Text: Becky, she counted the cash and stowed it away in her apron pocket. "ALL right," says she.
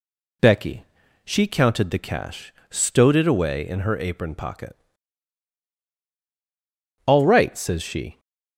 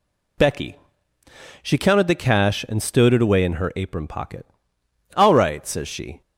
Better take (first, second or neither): second